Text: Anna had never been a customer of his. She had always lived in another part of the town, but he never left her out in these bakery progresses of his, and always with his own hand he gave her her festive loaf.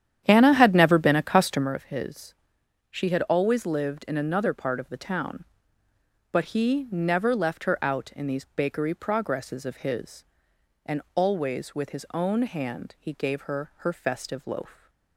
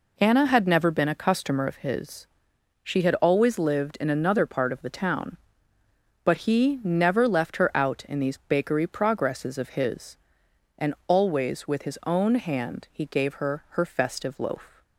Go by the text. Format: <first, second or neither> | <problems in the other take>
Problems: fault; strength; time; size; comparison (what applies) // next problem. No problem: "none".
second | starts louder than the rest; strong; until 1.7 s; 10 dB